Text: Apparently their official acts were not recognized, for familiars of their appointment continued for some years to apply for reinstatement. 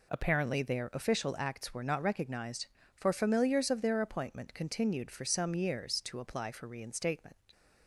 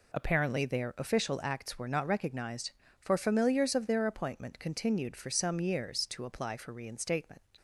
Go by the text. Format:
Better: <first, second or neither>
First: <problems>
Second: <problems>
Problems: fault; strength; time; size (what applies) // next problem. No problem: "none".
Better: neither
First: none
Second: none